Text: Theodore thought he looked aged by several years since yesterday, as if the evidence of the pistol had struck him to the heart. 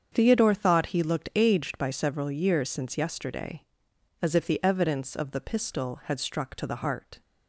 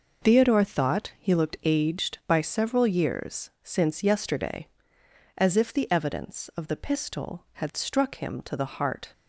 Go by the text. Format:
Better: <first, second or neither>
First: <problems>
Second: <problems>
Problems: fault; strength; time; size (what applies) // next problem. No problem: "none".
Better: second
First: starts louder than the rest; strong; until 1.1 s; 7.5 dB // skips "him"; at 6.5 s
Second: none